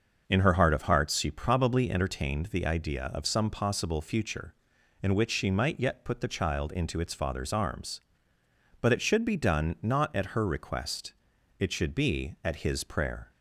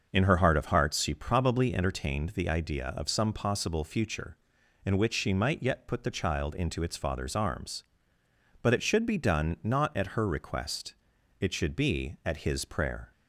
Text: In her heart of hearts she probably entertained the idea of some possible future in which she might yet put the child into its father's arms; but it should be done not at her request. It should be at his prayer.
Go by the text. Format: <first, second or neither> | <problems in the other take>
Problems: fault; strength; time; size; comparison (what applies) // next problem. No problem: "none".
neither | starts louder than the rest; noticeable; the same in both